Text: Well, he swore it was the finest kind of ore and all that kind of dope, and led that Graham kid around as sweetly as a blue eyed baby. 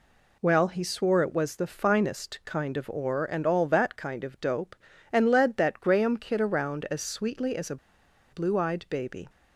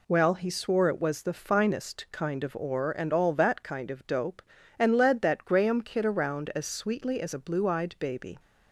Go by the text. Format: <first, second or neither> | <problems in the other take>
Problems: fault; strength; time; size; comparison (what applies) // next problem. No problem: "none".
second | pauses between "a" and "blue"; noticeable; at 7.7 s; 0.55 s long